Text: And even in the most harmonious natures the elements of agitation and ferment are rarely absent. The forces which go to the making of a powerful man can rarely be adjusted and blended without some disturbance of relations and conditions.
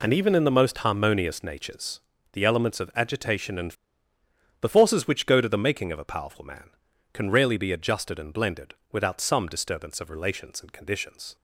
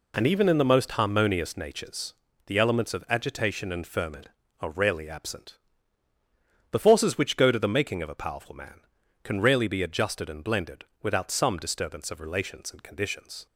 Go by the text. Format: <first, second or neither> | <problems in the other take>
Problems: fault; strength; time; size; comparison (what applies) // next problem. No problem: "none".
second | pauses between "natures" and "the"; slight; at 1.9 s; 0.34 s long; slight in the second // skips "ferment are rarely absent"; at 4.1 s // pauses between "blended" and "without"; slight; at 8.7 s; 0.18 s long; slight in the second